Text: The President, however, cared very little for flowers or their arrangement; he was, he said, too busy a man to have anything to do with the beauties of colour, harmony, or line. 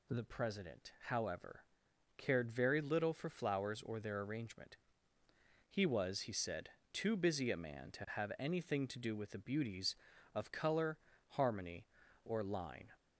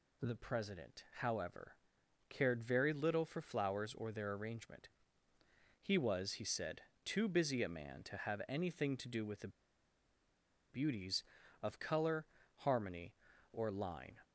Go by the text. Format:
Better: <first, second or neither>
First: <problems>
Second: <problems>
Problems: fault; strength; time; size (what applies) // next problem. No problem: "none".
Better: first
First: none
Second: pauses between "the" and "beauties"; at 9.4 s; 1.2 s long